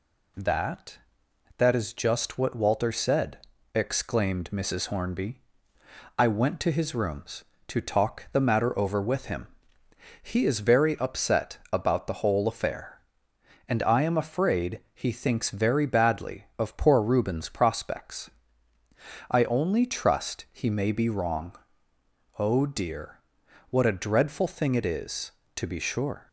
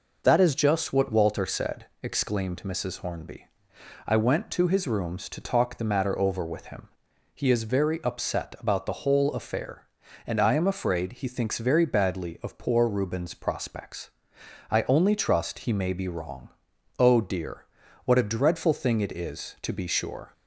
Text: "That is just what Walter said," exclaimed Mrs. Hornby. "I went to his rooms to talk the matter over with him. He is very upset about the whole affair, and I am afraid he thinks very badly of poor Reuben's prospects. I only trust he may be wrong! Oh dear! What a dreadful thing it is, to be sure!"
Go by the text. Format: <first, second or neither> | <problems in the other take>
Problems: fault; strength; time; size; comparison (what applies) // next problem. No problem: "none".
second | says "That" twice; at 1.5 s